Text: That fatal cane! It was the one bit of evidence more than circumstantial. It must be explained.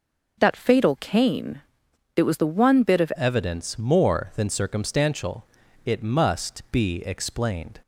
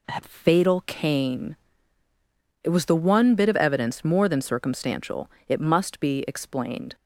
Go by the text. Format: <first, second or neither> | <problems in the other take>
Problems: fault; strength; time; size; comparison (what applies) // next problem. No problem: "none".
second | changes voice at "evidence"; from 3.1 s on; 4.7 s long